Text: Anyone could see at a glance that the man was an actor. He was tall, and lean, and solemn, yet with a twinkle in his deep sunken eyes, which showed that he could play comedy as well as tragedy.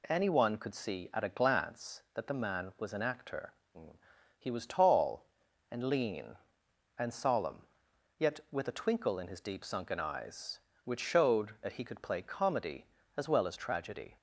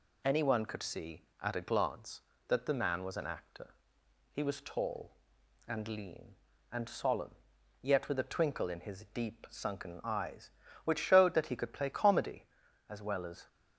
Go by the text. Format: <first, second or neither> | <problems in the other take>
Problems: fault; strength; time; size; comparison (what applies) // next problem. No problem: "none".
first | stops before "tragedy"; at 13.4 s